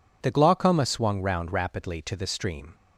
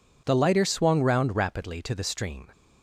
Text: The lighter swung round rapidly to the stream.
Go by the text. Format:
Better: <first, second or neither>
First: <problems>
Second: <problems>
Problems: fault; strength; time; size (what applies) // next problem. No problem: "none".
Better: second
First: says "glaucoma" for "lighter"; at 0.3 s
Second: none